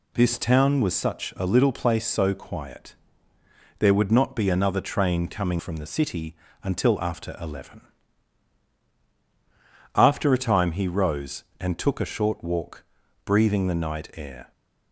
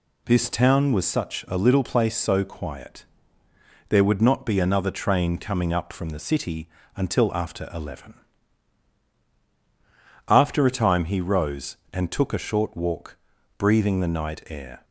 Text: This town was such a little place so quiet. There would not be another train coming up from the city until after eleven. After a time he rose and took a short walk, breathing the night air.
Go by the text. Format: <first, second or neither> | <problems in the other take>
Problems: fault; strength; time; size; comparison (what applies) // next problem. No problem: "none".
second | skips "up"; at 5.6 s // pauses between "city" and "until"; slight; at 6.3 s; 0.26 s long; slight in the second